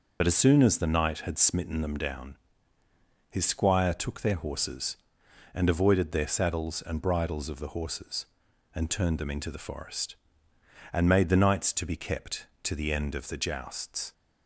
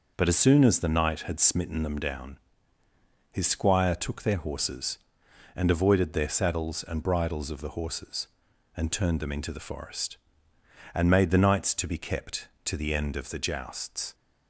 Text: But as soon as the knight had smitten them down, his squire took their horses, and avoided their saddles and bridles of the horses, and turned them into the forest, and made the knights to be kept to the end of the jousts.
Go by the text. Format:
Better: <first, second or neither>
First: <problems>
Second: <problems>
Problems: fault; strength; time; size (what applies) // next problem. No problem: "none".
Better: second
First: loses the start of "But"; at 0.2 s; 55 ms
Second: none